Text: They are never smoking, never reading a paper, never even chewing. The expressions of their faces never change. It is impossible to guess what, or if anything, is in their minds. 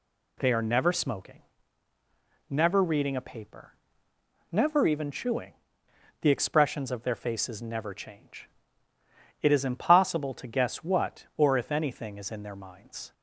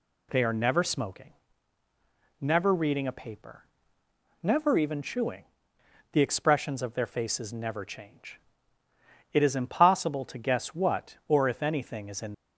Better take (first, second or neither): first